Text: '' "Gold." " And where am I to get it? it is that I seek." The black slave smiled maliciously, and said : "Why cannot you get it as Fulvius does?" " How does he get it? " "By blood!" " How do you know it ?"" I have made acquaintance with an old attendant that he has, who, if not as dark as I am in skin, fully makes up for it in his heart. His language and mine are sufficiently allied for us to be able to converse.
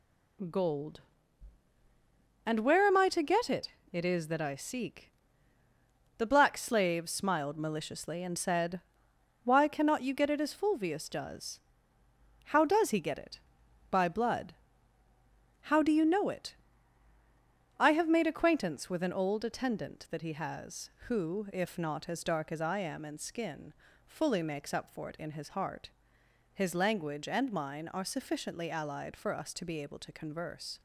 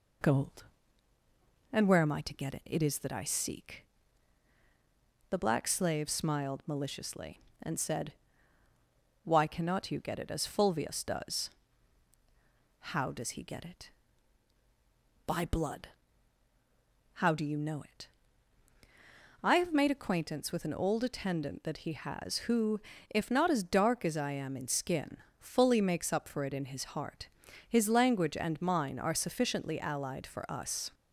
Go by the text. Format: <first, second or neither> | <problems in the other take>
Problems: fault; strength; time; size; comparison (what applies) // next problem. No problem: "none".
first | stops before "to be able to converse"; at 30.9 s